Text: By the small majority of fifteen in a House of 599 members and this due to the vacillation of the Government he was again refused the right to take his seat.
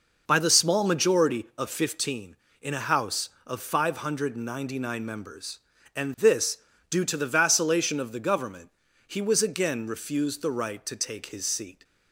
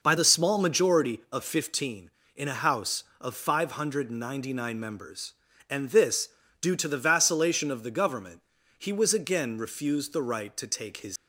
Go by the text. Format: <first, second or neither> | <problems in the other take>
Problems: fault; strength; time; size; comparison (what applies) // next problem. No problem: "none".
first | pauses between "this" and "due"; slight; at 6.2 s; 0.34 s long; slight in the first // pauses between "Government" and "he"; at 8.4 s; 0.38 s long; also in the first // stops before "seat"; at 11.1 s